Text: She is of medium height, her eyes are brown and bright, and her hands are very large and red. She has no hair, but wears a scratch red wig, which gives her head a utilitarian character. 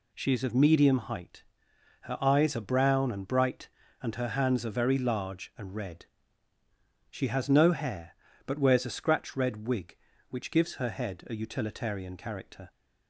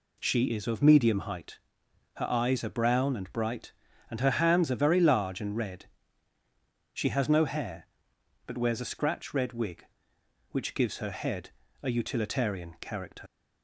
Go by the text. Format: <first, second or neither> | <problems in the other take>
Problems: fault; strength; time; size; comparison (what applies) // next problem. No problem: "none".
first | pauses between "head" and "a"; slight; at 11.5 s; 0.30 s long // leaves "character" unfinished; at 13.2 s; 55 ms